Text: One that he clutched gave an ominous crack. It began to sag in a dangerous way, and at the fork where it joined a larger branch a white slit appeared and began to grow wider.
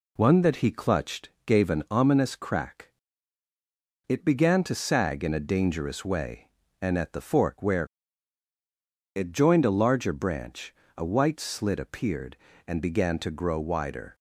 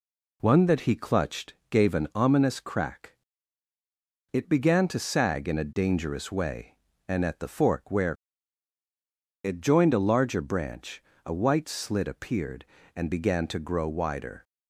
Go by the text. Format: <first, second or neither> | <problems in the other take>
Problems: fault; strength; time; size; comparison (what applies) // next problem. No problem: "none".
neither | pauses between "clutched" and "gave"; slight; the same in both // pauses between "where" and "it"; strong; the same in both // pauses between "branch" and "a"; slight; the same in both